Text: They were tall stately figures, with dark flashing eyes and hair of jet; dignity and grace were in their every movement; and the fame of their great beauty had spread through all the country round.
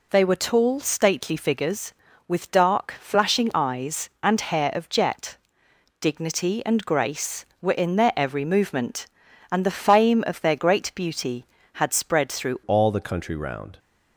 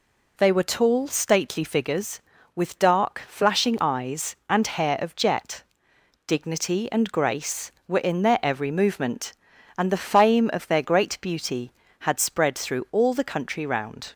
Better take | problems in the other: second | changes voice at "all"; from 12.6 s on; 1.1 s long

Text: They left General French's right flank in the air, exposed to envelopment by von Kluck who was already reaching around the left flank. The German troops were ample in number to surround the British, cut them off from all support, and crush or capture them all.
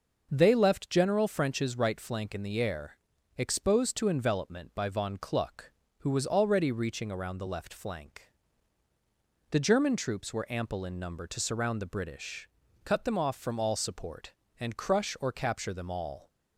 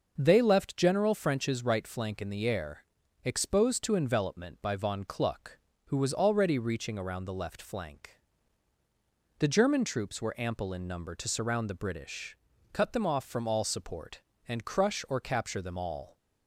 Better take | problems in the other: neither | none

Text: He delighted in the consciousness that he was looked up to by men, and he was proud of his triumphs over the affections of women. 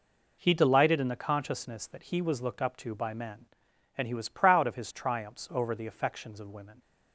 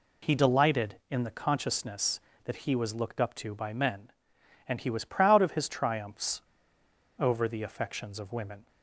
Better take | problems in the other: first | pauses between "triumphs" and "over"; noticeable; at 6.3 s; 0.79 s long

